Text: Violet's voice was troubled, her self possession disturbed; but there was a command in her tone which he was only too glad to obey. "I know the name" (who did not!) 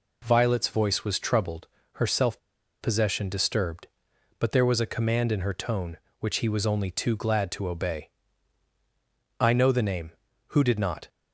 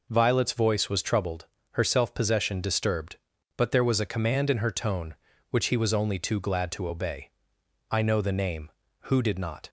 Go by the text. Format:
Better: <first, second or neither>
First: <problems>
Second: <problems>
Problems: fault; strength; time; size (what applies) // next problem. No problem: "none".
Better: second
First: pauses between "self" and "possession"; at 2.3 s; 0.42 s long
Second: none